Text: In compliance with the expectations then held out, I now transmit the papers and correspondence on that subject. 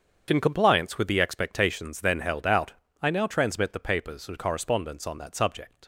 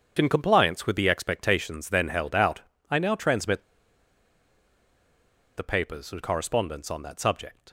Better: first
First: starts louder than the rest; strong; until 1.2 s; 7 dB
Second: starts louder than the rest; strong; until 1.1 s; 7 dB // pauses between "transmit" and "the"; strong; at 3.6 s; 1.9 s long

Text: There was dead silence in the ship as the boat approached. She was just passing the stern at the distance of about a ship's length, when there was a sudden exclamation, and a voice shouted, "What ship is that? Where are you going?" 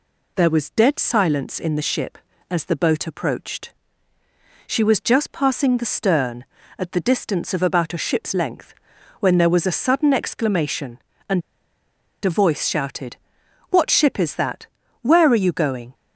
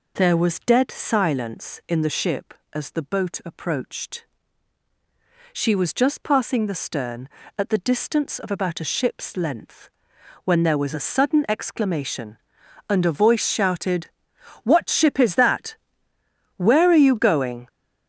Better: second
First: pauses between "and" and "a"; noticeable; at 11.4 s; 0.83 s long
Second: none

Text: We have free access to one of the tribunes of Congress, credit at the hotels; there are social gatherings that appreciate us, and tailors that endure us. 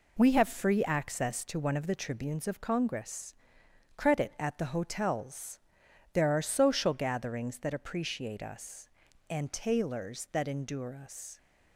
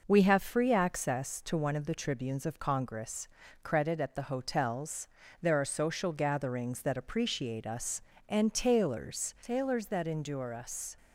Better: first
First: none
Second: says "tailors" twice; at 9.4 s

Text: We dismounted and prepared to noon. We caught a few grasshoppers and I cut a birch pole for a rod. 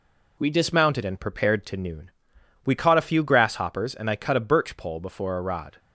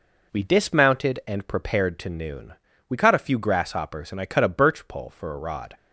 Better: second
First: says "before" for "for"; at 5.0 s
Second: none

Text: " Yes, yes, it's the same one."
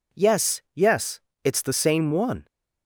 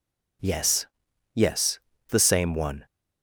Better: first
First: none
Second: skips "it's"; at 1.9 s

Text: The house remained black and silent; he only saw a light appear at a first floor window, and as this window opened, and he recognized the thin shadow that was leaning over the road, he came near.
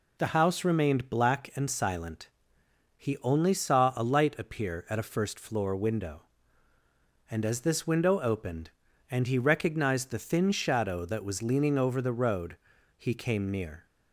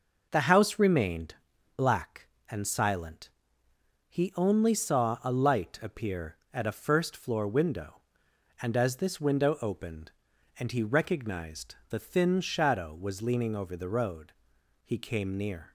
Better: first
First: none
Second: pauses between "remained" and "black"; at 1.3 s; 0.40 s long // skips "that"; at 12.9 s

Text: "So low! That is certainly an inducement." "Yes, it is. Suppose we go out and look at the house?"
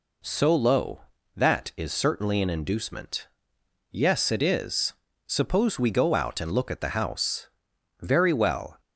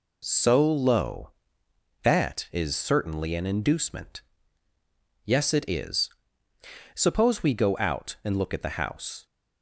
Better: second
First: goes on to say "Very well"; noticeable; from 7.9 s on; 0.80 s long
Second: none

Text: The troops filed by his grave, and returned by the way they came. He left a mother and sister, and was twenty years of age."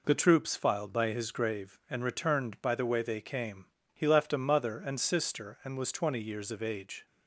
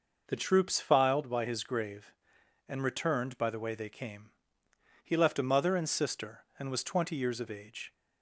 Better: neither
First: none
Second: none

